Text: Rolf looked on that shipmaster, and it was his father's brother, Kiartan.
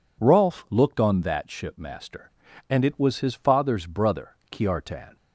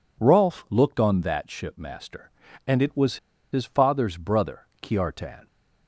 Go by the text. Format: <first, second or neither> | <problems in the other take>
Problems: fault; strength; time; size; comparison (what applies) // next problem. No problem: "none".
first | pauses between "was" and "his"; slight; at 3.1 s; 0.35 s long